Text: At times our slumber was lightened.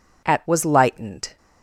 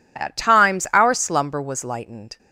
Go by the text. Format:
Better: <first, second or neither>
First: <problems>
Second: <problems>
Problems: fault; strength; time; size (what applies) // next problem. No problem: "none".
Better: second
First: skips "times our slumber"; at 0.4 s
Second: none